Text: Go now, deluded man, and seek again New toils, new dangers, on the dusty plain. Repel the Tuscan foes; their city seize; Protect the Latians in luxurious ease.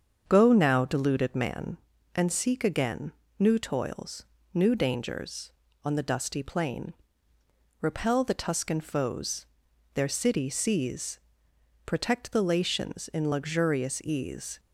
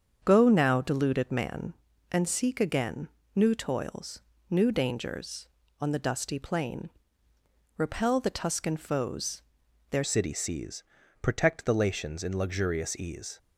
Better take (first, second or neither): first